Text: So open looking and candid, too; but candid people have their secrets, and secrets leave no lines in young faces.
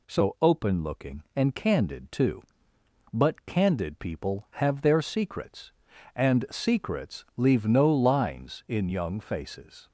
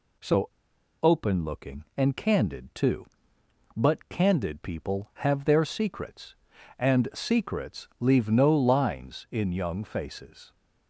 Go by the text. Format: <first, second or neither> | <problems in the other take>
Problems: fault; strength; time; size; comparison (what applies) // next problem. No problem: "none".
first | pauses between "So" and "open"; noticeable; at 0.4 s; 0.51 s long